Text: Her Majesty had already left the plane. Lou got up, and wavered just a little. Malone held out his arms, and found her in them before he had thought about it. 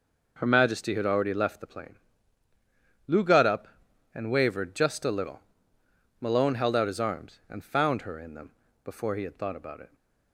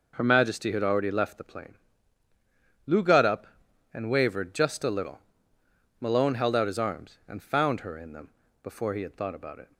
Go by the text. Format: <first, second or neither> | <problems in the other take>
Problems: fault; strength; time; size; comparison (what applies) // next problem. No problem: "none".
neither | pauses between "them" and "before"; slight; the same in both